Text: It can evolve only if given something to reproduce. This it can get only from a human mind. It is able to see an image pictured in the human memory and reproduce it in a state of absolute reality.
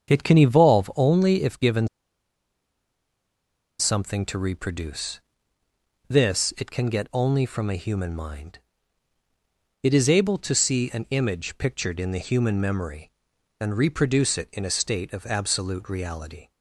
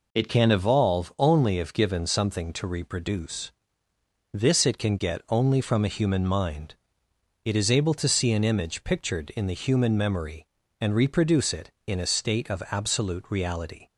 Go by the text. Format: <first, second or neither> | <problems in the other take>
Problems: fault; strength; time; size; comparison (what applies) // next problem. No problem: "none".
second | starts louder than the rest; strong; until 1.1 s; 7.5 dB // pauses between "given" and "something"; strong; at 1.8 s; 1.9 s long